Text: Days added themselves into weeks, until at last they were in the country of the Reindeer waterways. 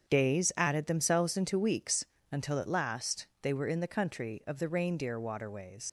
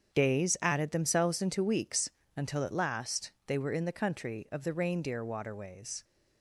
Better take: second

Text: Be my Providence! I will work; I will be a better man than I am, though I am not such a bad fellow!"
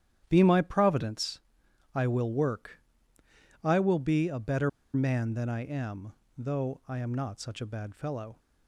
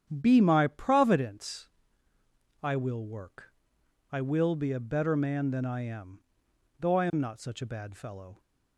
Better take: second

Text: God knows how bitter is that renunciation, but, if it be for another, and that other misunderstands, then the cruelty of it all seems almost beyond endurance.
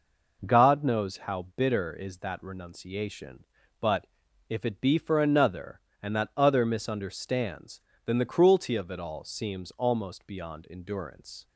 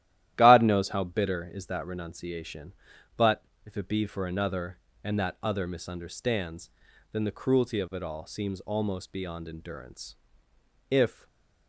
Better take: first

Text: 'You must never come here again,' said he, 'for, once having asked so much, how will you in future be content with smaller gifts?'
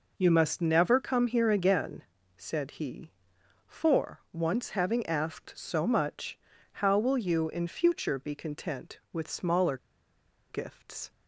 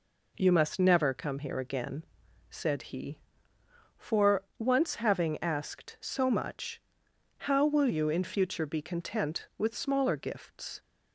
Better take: second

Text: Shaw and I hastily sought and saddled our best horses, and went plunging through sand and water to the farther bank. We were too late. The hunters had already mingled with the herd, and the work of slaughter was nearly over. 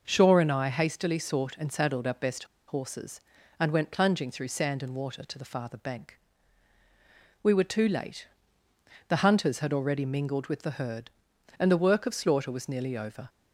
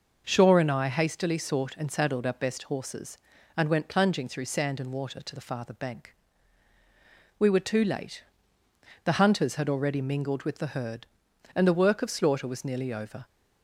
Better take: second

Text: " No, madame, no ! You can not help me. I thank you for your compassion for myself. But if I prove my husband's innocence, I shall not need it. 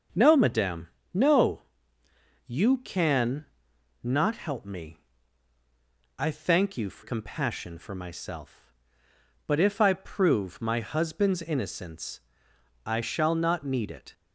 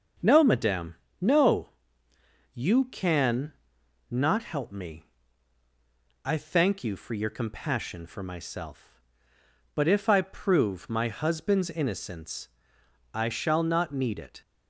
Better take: second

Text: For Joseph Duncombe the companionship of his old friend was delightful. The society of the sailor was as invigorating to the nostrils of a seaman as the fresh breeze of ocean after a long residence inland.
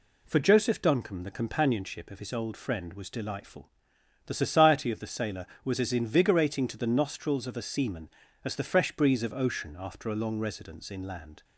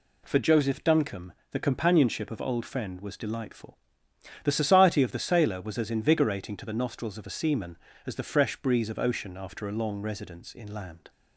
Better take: first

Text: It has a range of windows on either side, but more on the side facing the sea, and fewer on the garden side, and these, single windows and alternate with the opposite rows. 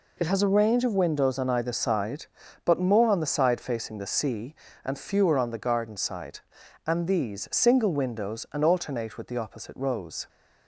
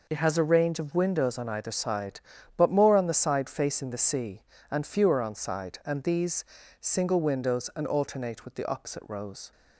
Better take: first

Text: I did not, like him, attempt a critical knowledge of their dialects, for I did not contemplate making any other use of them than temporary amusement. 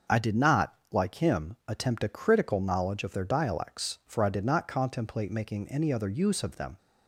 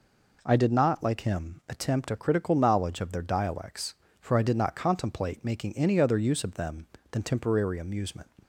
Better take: second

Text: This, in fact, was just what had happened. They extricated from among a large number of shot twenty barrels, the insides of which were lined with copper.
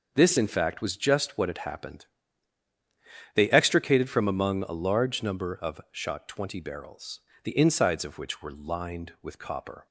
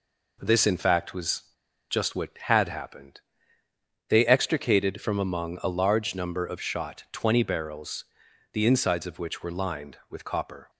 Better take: first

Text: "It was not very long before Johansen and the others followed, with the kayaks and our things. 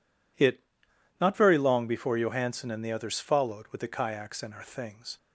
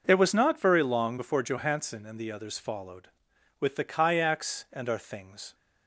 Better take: second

